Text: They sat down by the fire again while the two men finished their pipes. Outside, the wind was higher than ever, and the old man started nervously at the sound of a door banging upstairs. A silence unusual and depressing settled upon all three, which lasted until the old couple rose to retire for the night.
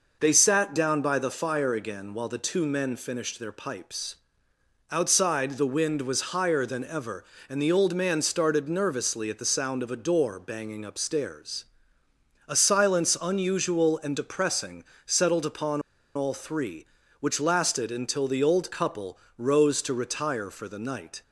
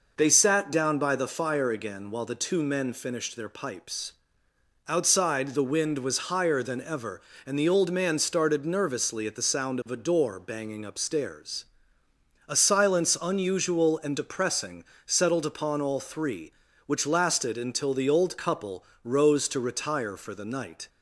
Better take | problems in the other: second | pauses between "depressing" and "settled"; slight; at 14.8 s; 0.24 s long; slight in the second // pauses between "upon" and "all"; slight; at 15.8 s; 0.35 s long // pauses between "couple" and "rose"; slight; at 19.1 s; 0.22 s long; slight in the second

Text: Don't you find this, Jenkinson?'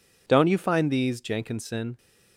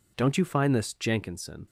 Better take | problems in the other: second | says "these" for "this"; at 0.9 s

